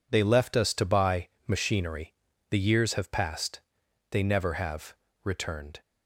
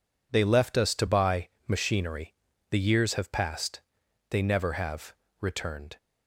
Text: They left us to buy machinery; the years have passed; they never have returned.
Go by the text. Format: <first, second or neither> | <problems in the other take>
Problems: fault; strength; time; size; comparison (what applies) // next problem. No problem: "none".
neither | pauses between "buy" and "machinery"; slight; the same in both // pauses between "have" and "returned"; slight; the same in both